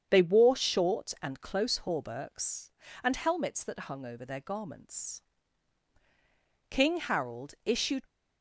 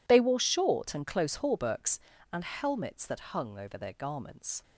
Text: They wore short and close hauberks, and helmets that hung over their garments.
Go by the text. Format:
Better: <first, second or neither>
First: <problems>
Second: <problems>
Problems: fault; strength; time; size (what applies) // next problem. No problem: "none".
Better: second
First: starts louder than the rest; strong; until 1.1 s; 8 dB // goes on to say "King Harold issued"; from 6.6 s on; 1.3 s long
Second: none